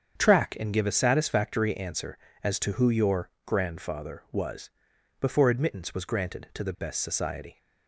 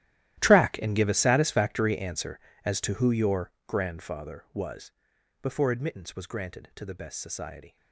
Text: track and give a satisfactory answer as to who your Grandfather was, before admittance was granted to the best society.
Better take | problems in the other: first | gets quieter; strong; throughout; 18.5 dB // starts louder than the rest; strong; until 1.4 s; 13.5 dB; strong in the first

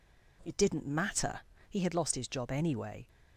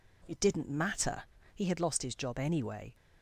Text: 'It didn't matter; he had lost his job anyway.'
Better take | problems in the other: neither | none

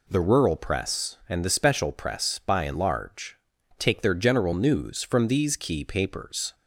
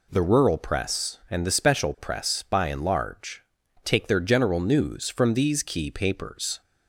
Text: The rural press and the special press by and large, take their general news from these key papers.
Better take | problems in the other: neither | none

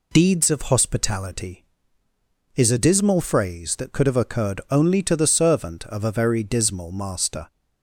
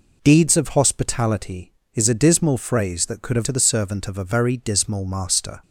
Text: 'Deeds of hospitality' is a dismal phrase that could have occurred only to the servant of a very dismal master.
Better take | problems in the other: first | skips "occurred only"; at 3.4 s

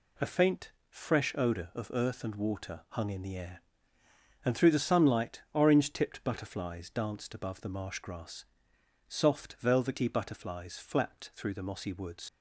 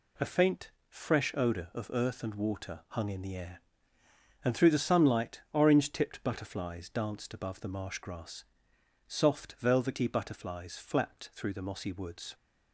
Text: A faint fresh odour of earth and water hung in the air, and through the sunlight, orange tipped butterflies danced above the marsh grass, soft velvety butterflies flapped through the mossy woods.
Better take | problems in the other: second | pauses between "faint" and "fresh"; slight; at 0.7 s; 0.18 s long; slight in the second // leaves "woods" unfinished; at 12.2 s; 65 ms

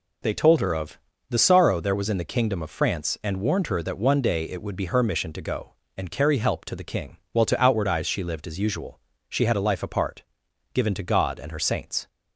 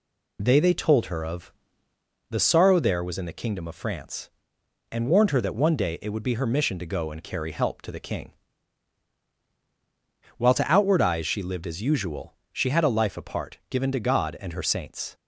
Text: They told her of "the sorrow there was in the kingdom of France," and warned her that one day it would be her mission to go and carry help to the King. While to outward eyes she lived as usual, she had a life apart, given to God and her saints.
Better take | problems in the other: first | says "They" twice; at 0.5 s // pauses between "of" and "the"; noticeable; at 1.5 s; 0.78 s long; slight in the first

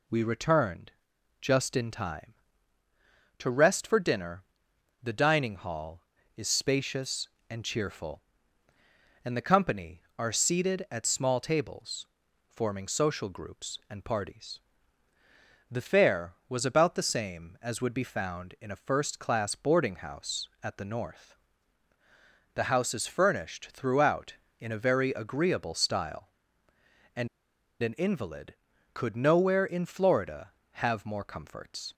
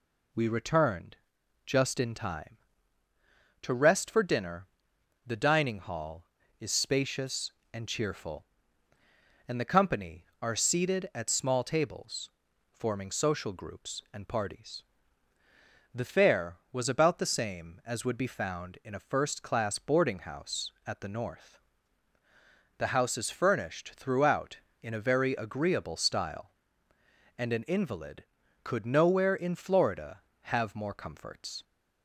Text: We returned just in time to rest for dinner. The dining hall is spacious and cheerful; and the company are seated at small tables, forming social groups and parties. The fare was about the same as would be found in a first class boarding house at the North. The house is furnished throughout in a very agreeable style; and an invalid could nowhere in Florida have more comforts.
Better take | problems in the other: second | pauses between "returned" and "just"; noticeable; at 0.9 s; 0.50 s long; noticeable in the second // pauses between "and" and "an"; noticeable; at 27.2 s; 0.53 s long

